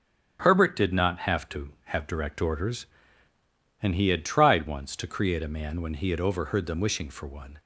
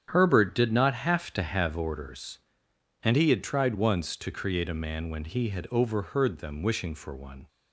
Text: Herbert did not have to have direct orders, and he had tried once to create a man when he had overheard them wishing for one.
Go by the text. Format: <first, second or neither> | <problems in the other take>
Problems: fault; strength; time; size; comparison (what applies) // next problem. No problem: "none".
first | starts louder than the rest; strong; until 1.1 s; 9 dB; also in the first // skips "direct"; at 1.7 s